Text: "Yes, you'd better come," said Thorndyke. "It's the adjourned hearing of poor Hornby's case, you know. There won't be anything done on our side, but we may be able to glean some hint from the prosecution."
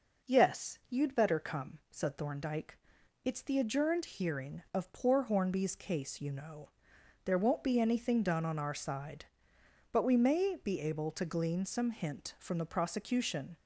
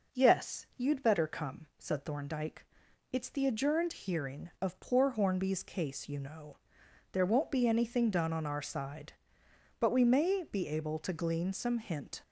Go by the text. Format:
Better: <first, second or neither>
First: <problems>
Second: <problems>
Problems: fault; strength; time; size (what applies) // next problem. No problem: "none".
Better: first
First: none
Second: stops before "from the prosecution"; at 12.2 s